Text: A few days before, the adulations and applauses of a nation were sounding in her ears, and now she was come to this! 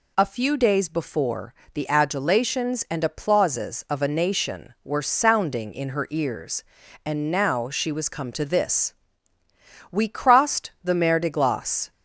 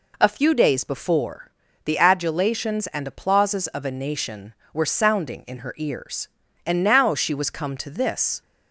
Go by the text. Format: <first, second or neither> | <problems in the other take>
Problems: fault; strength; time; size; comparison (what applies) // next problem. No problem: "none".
second | goes on to say "We crossed the Mer de Glace"; strong; from 9.8 s on; 2.0 s long